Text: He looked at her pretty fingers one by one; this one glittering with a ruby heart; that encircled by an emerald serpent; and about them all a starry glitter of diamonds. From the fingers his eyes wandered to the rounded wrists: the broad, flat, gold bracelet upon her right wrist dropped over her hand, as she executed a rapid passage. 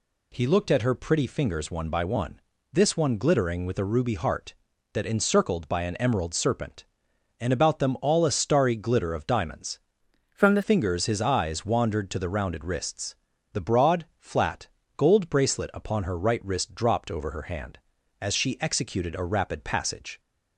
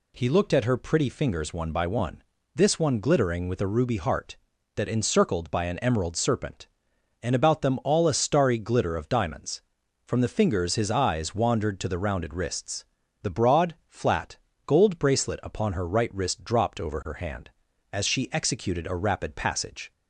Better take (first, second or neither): second